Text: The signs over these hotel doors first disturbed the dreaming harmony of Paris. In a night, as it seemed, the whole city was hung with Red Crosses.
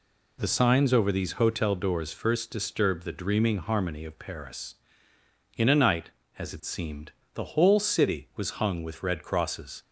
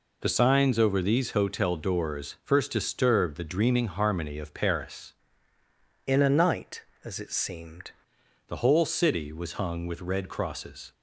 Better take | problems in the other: first | changes voice from "In" to "seemed"; from 6.0 to 7.9 s; 1.9 s long

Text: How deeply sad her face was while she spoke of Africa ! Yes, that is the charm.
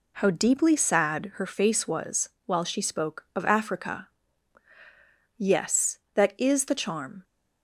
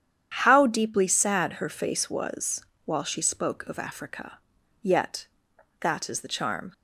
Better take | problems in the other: first | starts louder than the rest; strong; until 1.3 s; 9 dB // pauses between "was" and "while"; slight; at 2.6 s; 0.22 s long; slight in the first // says "Yet" for "Yes"; at 4.8 s

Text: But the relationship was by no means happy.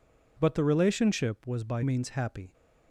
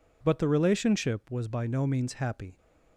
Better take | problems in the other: second | skips "no"; at 1.8 s

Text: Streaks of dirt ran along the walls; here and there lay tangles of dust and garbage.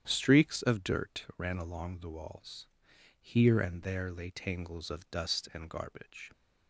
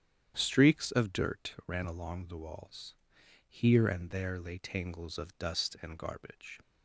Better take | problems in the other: neither | starts louder than the rest; strong; the same in both

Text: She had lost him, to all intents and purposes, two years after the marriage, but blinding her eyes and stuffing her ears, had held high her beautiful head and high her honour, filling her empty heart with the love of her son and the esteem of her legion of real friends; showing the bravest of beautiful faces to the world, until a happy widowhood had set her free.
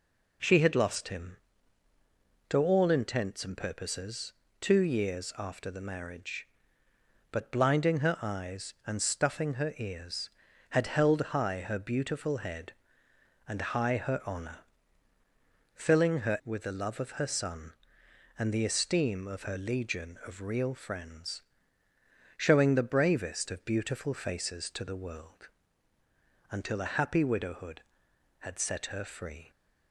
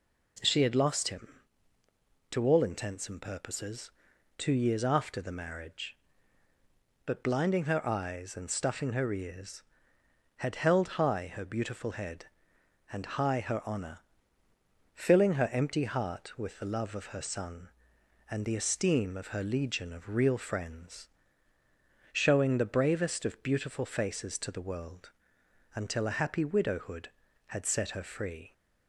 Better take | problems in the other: second | skips "empty heart"; at 16.4 s

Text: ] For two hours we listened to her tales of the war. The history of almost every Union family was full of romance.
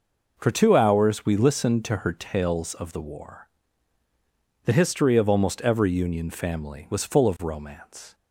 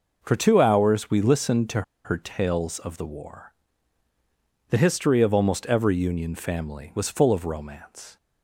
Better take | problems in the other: first | pauses between "to" and "her"; slight; at 1.8 s; 0.22 s long

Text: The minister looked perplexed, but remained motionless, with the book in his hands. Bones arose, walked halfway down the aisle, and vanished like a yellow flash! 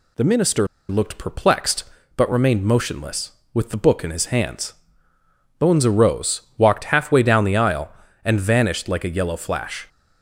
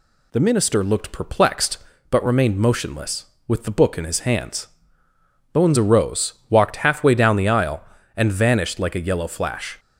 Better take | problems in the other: second | pauses between "minister" and "looked"; slight; at 0.6 s; 0.24 s long

